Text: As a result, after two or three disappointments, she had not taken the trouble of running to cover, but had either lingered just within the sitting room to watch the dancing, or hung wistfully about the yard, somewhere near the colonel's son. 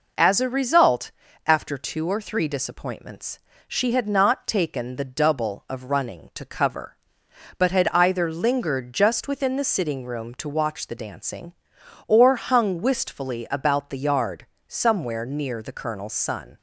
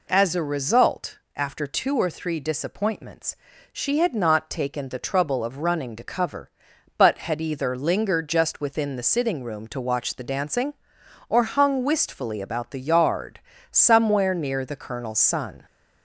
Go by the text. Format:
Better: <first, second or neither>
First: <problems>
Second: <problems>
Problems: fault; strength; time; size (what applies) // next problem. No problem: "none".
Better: second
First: says "double" for "trouble"; at 5.0 s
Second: none